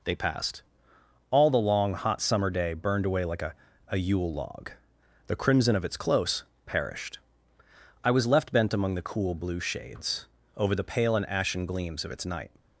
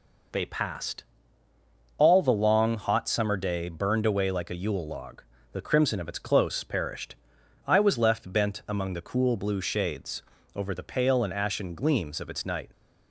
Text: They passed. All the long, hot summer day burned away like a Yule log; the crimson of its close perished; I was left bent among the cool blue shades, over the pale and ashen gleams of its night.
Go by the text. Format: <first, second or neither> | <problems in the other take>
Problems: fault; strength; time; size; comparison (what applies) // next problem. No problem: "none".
second | says "a" twice; at 3.9 s // pauses between "close" and "perished"; slight; at 6.4 s; 0.22 s long